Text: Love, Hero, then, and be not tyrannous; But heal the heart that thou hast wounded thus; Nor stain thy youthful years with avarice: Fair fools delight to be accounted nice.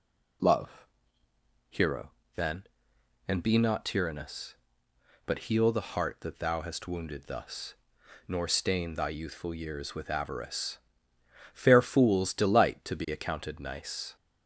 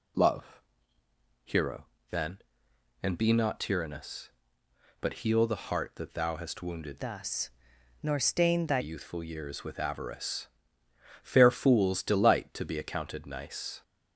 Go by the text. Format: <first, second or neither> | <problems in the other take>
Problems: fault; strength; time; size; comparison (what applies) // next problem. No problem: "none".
first | changes voice from "thus" to "thy"; from 7.0 to 8.7 s; 1.7 s long